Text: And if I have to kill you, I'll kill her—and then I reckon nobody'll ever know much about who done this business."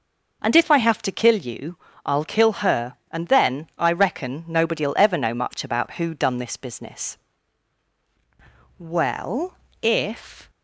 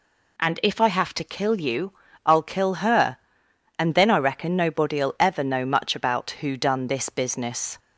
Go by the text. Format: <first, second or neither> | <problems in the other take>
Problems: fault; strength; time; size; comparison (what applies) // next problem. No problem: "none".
second | goes on to say "Well if"; strong; from 8.7 s on; 1.7 s long